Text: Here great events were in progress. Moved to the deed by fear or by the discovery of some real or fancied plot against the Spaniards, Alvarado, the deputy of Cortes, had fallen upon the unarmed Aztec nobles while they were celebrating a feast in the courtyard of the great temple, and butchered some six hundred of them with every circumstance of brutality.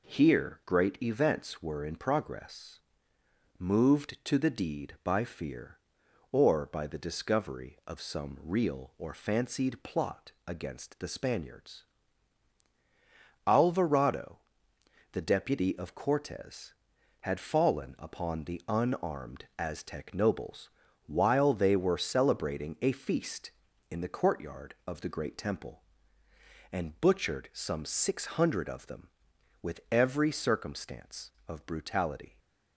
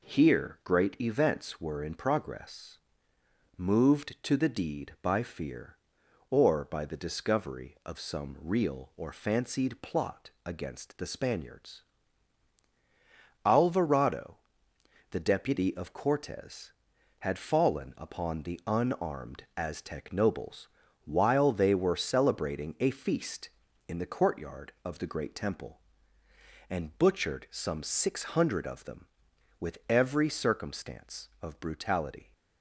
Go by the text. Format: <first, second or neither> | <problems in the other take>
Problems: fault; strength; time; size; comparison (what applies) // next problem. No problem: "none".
neither | pauses between "nobles" and "while"; the same in both